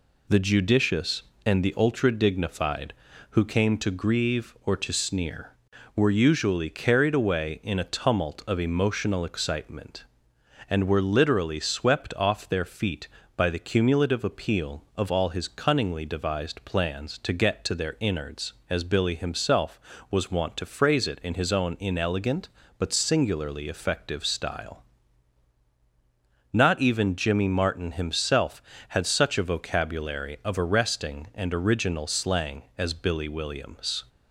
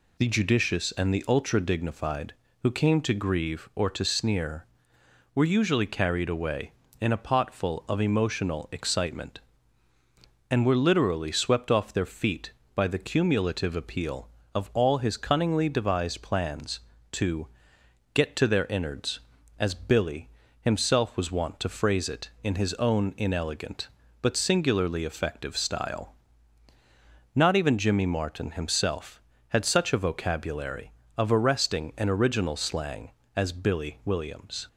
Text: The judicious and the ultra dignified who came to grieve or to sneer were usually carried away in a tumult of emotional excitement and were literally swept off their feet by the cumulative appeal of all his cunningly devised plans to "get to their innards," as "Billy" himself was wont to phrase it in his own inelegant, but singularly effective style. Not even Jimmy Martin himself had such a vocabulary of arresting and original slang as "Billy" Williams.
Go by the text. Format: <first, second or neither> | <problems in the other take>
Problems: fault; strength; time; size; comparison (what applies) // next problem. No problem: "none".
first | says "potful" for "tumult"; at 7.1 s // pauses between "to" and "get"; noticeable; at 17.4 s; 0.70 s long // pauses between "Billy" and "himself"; slight; at 20.2 s; 0.32 s long